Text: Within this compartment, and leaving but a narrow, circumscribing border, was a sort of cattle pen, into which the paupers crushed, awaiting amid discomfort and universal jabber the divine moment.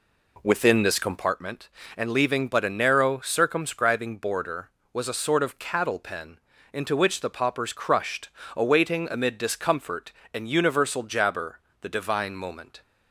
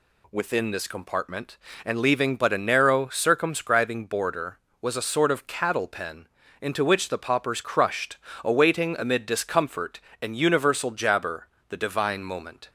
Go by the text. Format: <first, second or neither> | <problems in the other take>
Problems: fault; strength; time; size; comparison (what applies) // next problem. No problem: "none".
second | starts louder than the rest; slight; until 1.4 s; 3 dB // pauses between "jabber" and "the"; slight; at 11.5 s; 0.22 s long; slight in the second